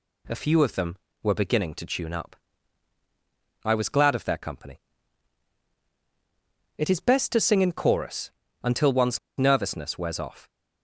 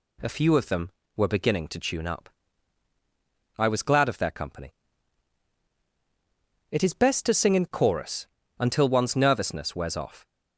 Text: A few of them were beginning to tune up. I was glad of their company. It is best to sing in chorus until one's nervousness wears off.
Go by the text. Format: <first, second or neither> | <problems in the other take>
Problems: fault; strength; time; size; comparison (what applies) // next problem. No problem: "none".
second | pauses between "chorus" and "until"; slight; at 8.2 s; 0.32 s long; slight in the second // pauses between "one's" and "nervousness"; slight; at 9.1 s; 0.19 s long